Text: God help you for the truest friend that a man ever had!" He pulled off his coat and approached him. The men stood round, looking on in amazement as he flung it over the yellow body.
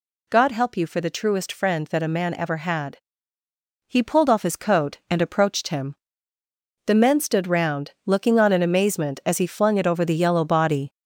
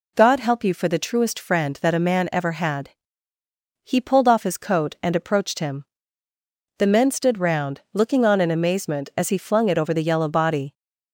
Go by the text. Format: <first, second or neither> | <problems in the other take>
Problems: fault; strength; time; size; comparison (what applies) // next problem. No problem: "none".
second | gets louder; noticeable; throughout; 5.5 dB